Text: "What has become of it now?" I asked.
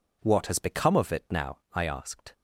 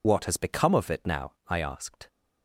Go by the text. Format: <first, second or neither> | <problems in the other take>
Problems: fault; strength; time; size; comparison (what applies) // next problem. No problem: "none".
first | loses the start of "What"; at 0.0 s; 55 ms